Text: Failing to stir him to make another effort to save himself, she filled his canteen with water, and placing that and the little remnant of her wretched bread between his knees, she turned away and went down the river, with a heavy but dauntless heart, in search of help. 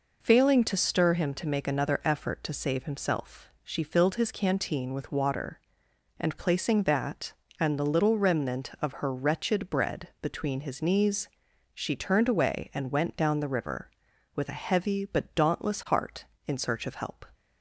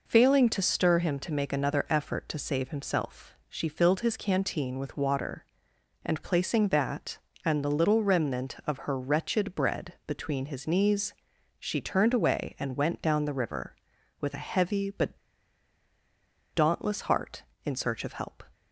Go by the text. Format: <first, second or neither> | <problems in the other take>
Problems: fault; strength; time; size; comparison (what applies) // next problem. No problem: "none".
first | pauses between "but" and "dauntless"; strong; at 15.1 s; 1.3 s long